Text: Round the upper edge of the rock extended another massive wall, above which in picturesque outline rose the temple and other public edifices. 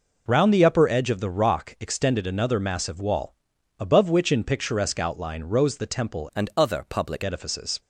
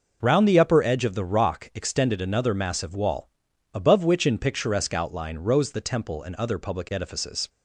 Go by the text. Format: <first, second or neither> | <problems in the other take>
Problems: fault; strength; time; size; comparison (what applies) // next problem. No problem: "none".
second | changes voice from "and" to "public"; from 6.3 to 7.2 s; 0.9 s long